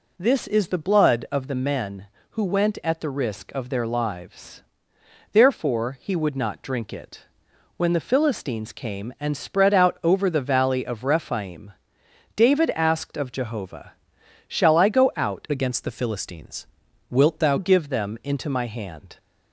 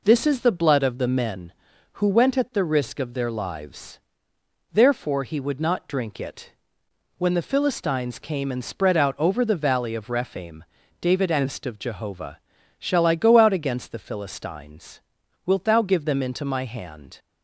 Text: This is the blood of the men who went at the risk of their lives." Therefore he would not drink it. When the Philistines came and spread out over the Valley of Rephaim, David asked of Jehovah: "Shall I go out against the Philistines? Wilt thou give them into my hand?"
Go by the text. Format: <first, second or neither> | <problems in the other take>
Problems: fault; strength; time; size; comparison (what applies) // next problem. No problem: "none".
second | changes voice from "against" to "thou"; from 15.5 to 17.5 s; 2.0 s long